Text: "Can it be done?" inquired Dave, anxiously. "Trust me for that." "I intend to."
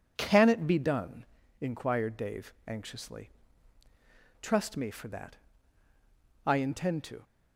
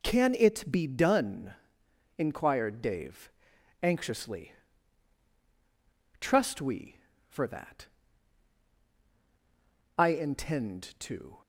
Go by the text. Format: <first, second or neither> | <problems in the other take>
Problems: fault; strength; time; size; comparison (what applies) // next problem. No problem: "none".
first | says "we" for "me"; at 6.6 s